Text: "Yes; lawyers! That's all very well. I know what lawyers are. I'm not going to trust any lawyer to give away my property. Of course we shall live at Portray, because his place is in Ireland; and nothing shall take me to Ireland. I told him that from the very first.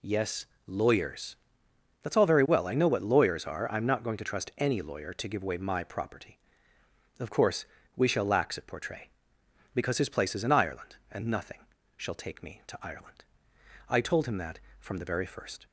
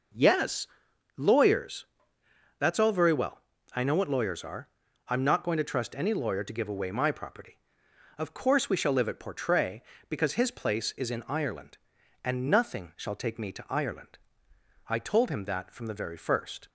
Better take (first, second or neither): second